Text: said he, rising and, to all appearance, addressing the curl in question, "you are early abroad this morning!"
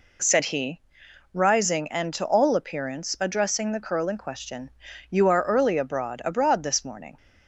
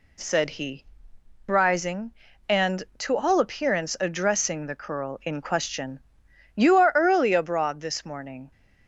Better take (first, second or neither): second